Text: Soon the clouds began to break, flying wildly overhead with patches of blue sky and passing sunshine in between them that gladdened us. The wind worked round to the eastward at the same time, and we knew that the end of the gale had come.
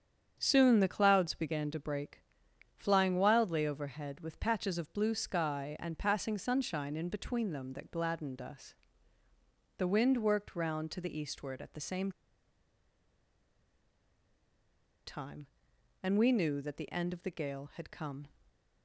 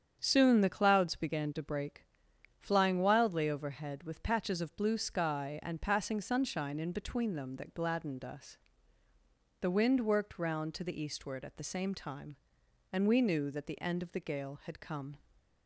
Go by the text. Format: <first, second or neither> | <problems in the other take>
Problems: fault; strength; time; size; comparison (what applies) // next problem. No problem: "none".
second | starts louder than the rest; strong; until 1.3 s; 8 dB; strong in the second // pauses between "same" and "time"; strong; at 12.1 s; 2.9 s long